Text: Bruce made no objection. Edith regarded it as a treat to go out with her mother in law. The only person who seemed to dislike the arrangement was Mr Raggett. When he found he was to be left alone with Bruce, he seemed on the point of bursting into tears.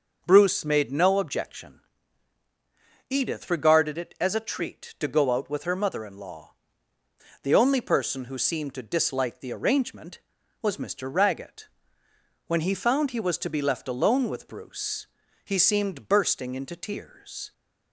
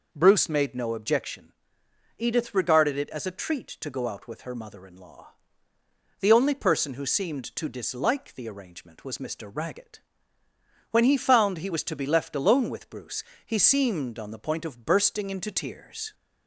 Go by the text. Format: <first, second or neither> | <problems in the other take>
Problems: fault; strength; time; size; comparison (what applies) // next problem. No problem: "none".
second | starts louder than the rest; until 1.2 s; 6.5 dB // skips "on the point of"; at 16.0 s